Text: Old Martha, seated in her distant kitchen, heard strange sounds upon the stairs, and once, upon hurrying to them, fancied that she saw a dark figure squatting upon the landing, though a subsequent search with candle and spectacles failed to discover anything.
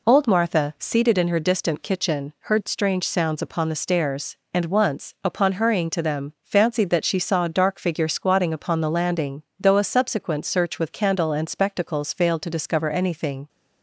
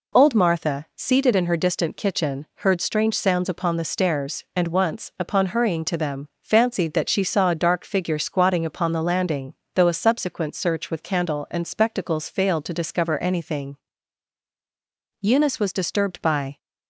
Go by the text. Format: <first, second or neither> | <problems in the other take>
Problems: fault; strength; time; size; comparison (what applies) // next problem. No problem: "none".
first | goes on to say "Eunice was disturbed by"; from 15.2 s on; 1.3 s long